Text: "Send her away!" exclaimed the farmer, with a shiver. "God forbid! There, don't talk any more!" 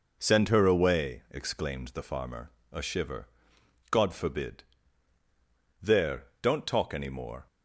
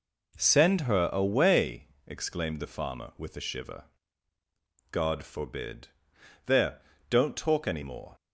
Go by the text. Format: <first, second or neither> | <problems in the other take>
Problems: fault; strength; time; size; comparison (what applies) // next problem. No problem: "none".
second | skips "with"; at 2.6 s